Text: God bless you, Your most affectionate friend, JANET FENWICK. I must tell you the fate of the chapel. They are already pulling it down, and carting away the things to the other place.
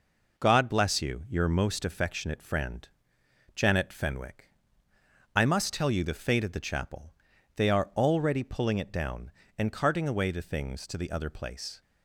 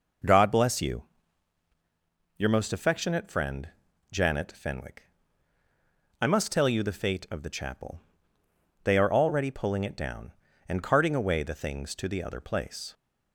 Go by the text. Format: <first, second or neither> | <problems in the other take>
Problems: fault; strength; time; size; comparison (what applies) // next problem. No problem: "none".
neither | none